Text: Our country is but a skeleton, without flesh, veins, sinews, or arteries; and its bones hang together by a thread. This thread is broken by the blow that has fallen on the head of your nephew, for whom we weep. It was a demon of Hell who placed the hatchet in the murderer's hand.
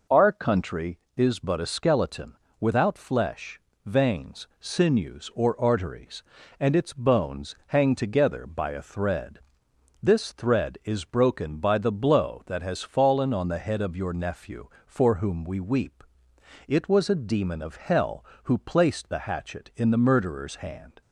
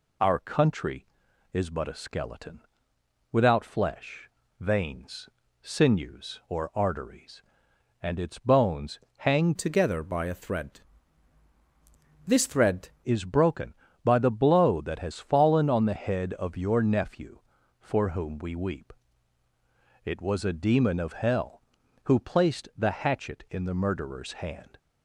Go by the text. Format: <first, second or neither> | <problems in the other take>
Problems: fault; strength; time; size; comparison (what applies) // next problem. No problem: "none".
first | pauses between "bones" and "hang"; slight; at 9.0 s; 0.16 s long // changes voice from "together" to "thread"; from 9.5 to 12.8 s; 3.3 s long